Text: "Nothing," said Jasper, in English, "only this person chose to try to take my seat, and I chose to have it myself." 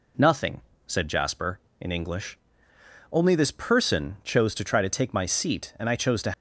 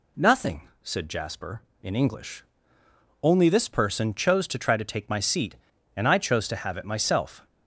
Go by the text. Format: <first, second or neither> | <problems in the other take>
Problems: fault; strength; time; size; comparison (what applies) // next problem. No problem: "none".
second | stops before "have it myself"; at 6.3 s